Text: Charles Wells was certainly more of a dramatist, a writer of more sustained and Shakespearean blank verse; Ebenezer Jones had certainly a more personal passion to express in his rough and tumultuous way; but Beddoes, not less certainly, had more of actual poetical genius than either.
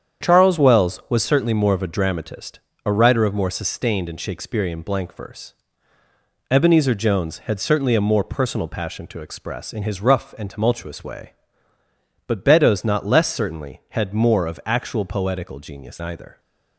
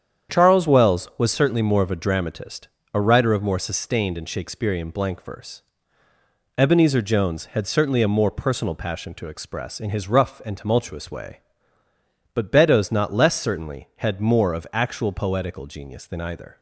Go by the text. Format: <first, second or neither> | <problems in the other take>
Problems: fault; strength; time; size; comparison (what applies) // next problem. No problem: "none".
second | starts louder than the rest; strong; until 1.3 s; 8 dB; strong in the second // skips "than"; at 15.9 s